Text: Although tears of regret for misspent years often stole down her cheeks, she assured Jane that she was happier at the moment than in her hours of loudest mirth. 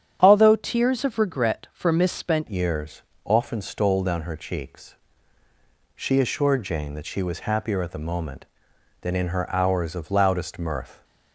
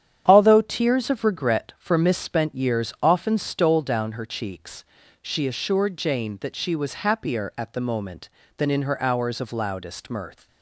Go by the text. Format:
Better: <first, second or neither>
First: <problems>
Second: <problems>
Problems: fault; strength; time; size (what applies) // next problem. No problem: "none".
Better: second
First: starts louder than the rest; strong; until 1.2 s; 9.5 dB // changes voice at "years"; from 2.4 s on; 8.6 s long // pauses between "years" and "often"; slight; at 3.0 s; 0.20 s long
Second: starts louder than the rest; strong; until 1.2 s; 9 dB